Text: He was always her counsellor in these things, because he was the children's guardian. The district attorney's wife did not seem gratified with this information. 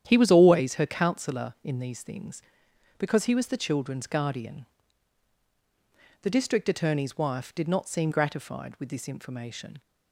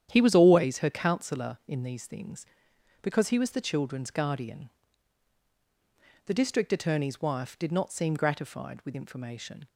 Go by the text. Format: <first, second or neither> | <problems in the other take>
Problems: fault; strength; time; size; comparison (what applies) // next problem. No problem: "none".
first | starts louder than the rest; strong; until 1.1 s; 9.5 dB; strong in the first // skips "this"; at 8.9 s